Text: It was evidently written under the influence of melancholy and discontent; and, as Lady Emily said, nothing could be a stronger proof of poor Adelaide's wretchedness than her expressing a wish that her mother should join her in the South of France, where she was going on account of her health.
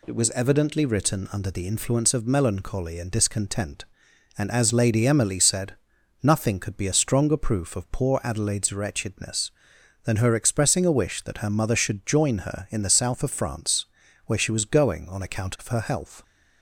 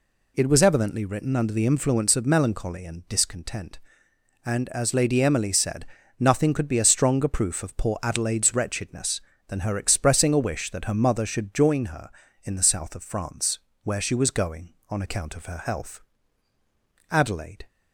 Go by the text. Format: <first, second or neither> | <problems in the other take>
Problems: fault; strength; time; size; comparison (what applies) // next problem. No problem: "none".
first | goes on to say "Adelaide"; from 17.1 s on; 0.56 s long